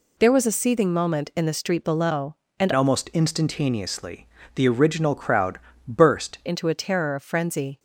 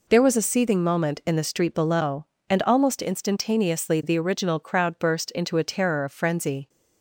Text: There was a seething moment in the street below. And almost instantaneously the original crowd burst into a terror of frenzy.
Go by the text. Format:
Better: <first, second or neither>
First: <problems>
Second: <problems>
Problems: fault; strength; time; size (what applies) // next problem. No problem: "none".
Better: second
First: changes voice from "almost" to "burst"; from 2.7 to 6.3 s; 3.6 s long // pauses between "instantaneously" and "the"; slight; at 4.2 s; 0.28 s long // pauses between "crowd" and "burst"; slight; at 5.5 s; 0.28 s long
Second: none